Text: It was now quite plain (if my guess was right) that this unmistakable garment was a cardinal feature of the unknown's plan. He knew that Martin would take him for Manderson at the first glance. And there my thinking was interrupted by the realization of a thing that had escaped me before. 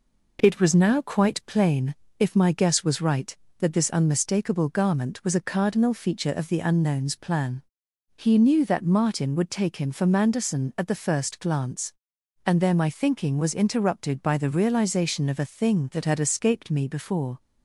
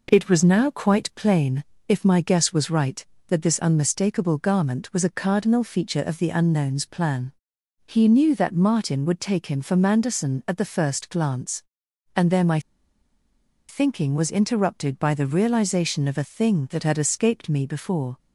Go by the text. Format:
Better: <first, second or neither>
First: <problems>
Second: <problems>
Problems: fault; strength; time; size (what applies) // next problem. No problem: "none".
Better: first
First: none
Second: pauses between "my" and "thinking"; at 12.5 s; 1.0 s long